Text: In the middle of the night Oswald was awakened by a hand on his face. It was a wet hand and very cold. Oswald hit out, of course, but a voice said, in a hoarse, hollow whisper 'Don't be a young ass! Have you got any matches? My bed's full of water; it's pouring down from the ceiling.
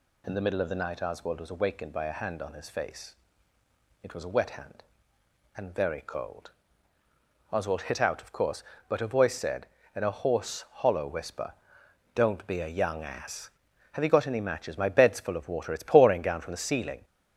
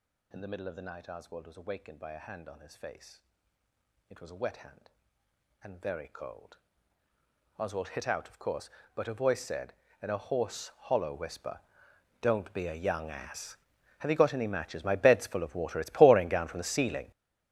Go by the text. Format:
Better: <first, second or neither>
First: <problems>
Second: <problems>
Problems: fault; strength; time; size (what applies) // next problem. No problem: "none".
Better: first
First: pauses between "whisper" and "Don't"; noticeable; at 11.5 s; 0.62 s long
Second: gets louder; strong; throughout; 14.5 dB // pauses between "whisper" and "Don't"; noticeable; at 11.5 s; 0.62 s long